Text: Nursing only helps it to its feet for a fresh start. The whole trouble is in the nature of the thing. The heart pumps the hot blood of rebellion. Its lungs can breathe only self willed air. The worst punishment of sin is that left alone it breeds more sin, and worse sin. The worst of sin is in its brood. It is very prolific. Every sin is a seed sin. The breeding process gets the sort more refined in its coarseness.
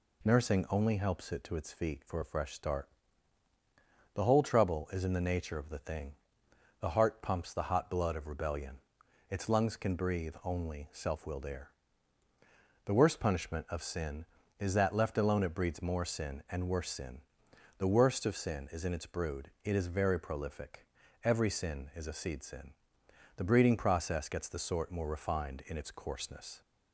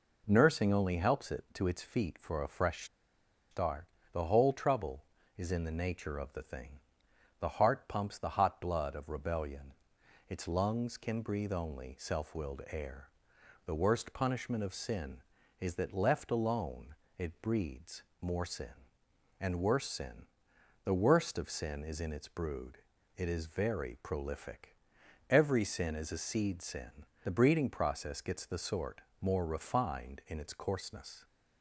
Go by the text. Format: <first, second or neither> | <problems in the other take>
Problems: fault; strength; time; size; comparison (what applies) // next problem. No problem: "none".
first | pauses between "fresh" and "start"; noticeable; at 2.8 s; 0.66 s long // pauses between "alone" and "it"; slight; at 16.9 s; 0.24 s long // pauses between "breeds" and "more"; slight; at 18.0 s; 0.20 s long // pauses between "sort" and "more"; slight; at 29.0 s; 0.18 s long